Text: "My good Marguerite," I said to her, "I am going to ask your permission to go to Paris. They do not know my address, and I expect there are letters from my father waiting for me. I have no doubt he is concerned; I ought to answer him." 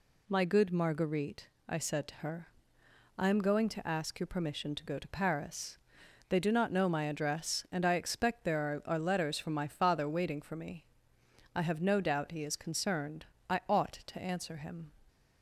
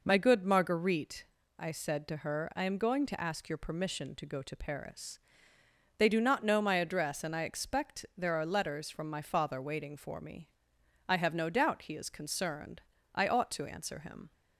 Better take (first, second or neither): second